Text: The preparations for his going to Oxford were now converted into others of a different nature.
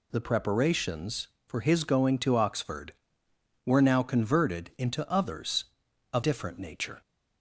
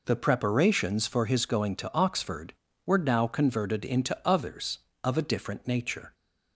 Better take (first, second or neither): second